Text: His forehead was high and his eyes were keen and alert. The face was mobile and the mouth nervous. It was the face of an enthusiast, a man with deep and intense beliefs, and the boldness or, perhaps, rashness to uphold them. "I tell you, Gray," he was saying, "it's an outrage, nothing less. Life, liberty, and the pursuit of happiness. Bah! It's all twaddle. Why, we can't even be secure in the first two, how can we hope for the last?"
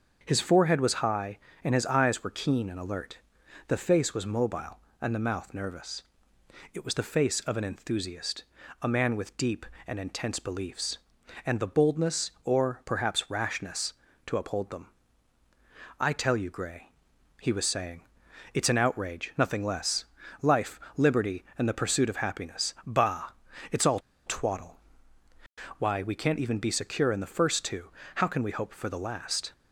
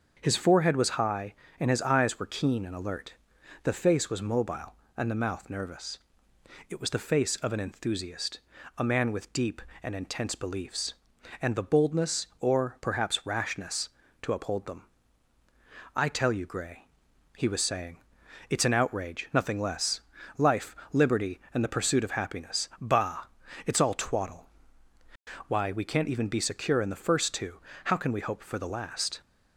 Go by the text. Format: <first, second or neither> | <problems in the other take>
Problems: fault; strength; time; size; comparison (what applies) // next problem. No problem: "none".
second | starts louder than the rest; until 1.2 s; 7 dB; also in the second // pauses between "all" and "twaddle"; slight; at 23.9 s; 0.28 s long